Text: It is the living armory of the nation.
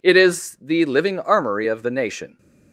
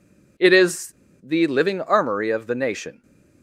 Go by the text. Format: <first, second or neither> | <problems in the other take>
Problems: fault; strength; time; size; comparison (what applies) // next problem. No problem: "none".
first | pauses between "is" and "the"; slight; at 0.9 s; 0.29 s long